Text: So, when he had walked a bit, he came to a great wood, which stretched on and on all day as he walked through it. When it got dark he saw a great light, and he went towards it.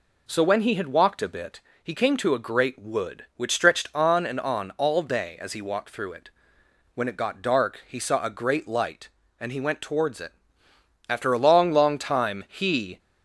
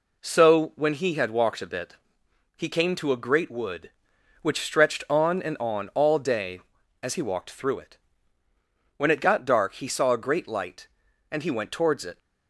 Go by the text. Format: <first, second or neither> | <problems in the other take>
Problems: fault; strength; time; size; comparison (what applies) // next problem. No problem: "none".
second | goes on to say "After a long long time he"; strong; from 11.0 s on; 1.9 s long